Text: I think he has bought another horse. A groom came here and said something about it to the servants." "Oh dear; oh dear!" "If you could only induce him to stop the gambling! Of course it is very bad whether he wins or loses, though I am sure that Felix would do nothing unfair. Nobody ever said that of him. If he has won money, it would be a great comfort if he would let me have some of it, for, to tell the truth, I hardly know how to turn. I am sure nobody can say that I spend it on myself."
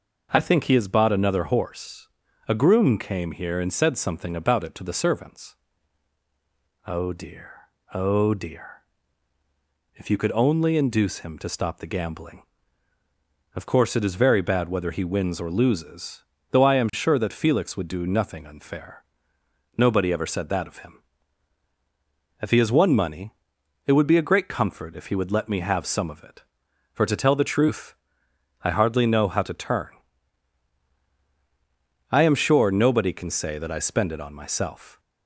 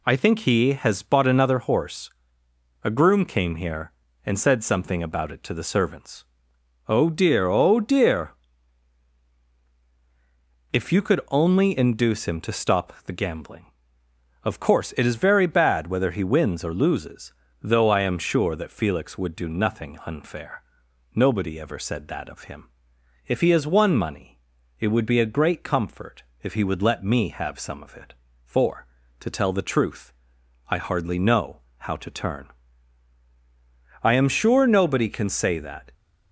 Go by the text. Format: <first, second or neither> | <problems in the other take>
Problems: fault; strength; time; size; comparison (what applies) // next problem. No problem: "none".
first | pauses between "comfort" and "if"; slight; at 26.2 s; 0.20 s long // pauses between "know" and "how"; slight; at 31.6 s; 0.18 s long // stops before "I spend it on myself"; at 35.9 s